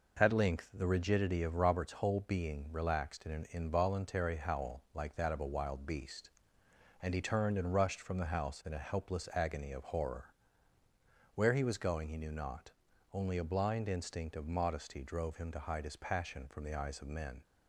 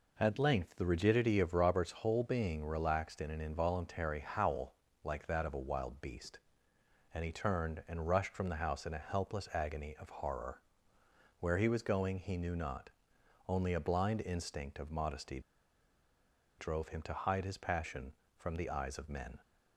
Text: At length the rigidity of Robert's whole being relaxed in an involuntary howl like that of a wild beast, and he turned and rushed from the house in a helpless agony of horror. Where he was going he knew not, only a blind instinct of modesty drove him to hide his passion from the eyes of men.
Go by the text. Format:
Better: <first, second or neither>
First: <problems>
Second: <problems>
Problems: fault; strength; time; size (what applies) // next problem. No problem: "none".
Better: first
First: none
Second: pauses between "howl" and "like"; slight; at 4.7 s; 0.28 s long // pauses between "modesty" and "drove"; at 15.3 s; 1.1 s long